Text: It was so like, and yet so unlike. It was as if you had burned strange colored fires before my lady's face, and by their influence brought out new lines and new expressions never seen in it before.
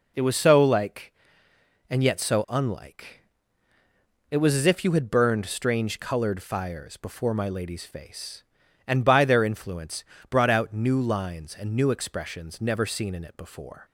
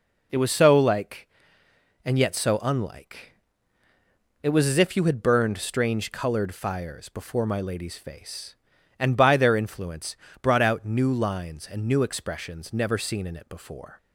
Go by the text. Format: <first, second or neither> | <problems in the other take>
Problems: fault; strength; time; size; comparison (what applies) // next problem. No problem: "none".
neither | pauses between "influence" and "brought"; slight; the same in both